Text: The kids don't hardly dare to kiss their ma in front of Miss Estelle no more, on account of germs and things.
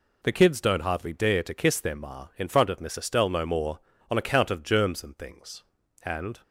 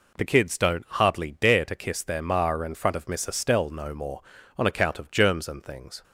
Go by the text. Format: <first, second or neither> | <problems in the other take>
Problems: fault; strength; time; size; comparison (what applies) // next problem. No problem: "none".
second | goes on to say "And"; slight; from 6.0 s on; 0.38 s long